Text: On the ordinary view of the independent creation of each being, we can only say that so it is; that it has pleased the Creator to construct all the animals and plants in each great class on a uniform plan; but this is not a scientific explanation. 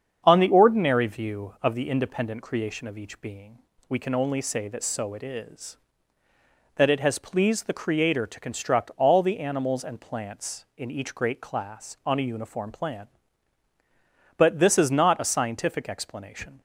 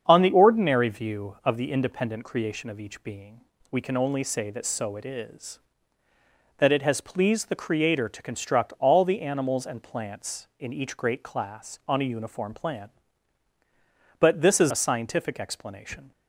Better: first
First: starts louder than the rest; strong; until 1.2 s; 7.5 dB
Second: starts louder than the rest; strong; until 1.0 s; 7.5 dB // skips "not"; at 14.7 s

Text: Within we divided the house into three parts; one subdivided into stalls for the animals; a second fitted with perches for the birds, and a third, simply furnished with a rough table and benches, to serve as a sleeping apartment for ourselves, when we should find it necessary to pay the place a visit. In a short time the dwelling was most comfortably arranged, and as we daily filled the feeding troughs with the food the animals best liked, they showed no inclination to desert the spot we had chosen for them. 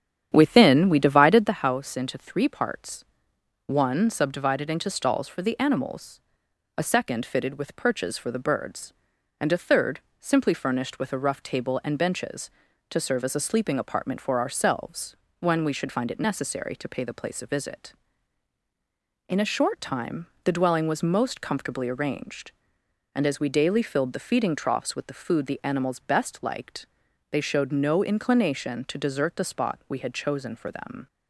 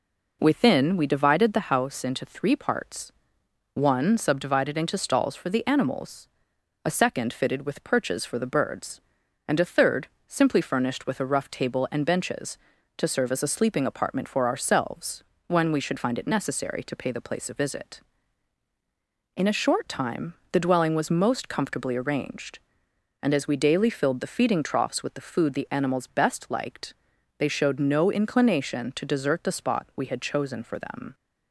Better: second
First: starts louder than the rest; strong; until 1.5 s; 9 dB // pauses between "time" and "the"; slight; at 20.2 s; 0.20 s long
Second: pauses between "time" and "the"; slight; at 20.3 s; 0.20 s long

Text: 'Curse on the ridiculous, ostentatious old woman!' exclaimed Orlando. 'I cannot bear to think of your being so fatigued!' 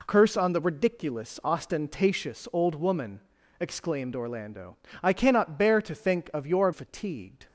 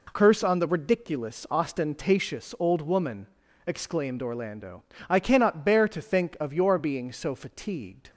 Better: second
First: skips "being so"; at 6.7 s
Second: none

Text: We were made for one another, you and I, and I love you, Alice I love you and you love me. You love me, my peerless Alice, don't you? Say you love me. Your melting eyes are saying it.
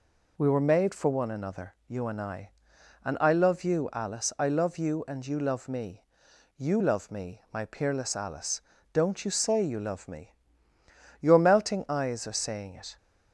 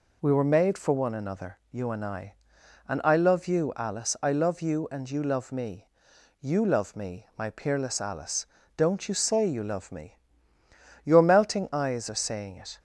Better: neither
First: none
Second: none

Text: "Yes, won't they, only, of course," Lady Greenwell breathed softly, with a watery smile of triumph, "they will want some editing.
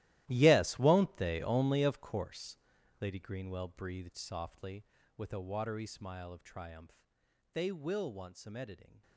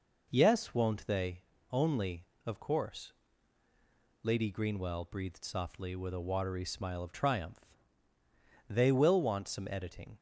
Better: second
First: gets quieter; strong; throughout; 15.5 dB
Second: none

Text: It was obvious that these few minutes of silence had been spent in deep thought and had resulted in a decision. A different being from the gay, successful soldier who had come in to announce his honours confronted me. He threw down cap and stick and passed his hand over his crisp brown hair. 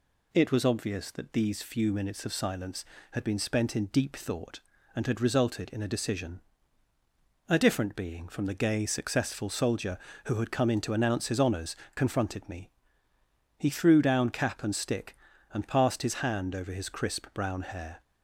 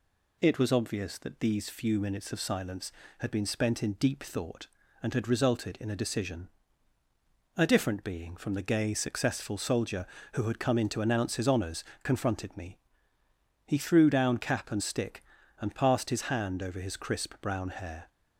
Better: neither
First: pauses between "honours" and "confronted"; slight; at 11.7 s; 0.22 s long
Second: pauses between "honours" and "confronted"; slight; at 11.8 s; 0.22 s long

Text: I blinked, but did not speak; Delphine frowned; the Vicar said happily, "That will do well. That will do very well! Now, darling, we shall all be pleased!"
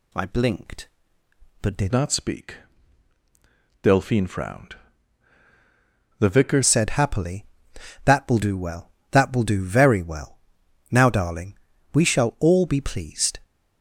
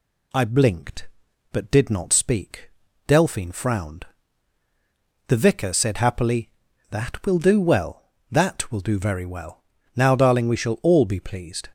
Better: second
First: changes voice from "not" to "Vicar"; from 1.9 to 6.6 s; 4.7 s long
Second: none

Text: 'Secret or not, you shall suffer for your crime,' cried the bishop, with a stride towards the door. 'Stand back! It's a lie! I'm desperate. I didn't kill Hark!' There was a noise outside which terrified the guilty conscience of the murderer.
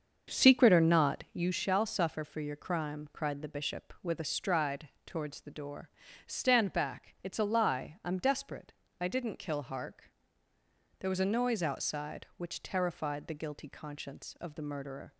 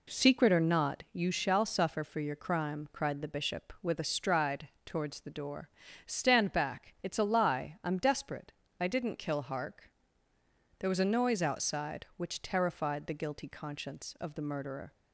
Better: second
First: starts louder than the rest; until 1.6 s; 6.5 dB // pauses between "stride" and "towards"; slight; at 4.8 s; 0.18 s long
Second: pauses between "stride" and "towards"; slight; at 4.6 s; 0.18 s long

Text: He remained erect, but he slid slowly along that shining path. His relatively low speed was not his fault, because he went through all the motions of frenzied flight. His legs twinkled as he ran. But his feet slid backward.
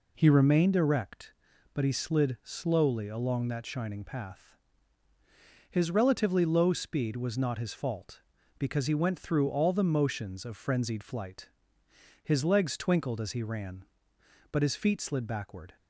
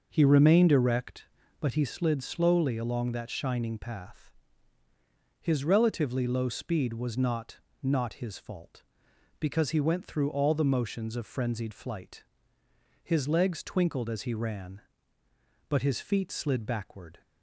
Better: first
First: none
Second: starts louder than the rest; noticeable; until 1.1 s; 6 dB // says "not" twice; at 7.8 s

